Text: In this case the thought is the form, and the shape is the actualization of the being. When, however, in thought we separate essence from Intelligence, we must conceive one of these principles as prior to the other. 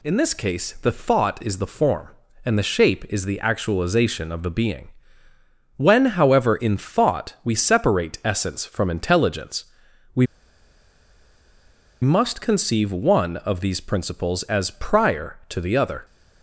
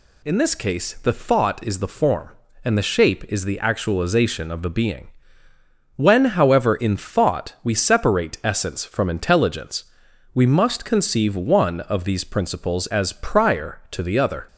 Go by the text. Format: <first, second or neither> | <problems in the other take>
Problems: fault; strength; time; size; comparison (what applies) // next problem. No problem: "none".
second | pauses between "we" and "must"; strong; at 10.2 s; 1.7 s long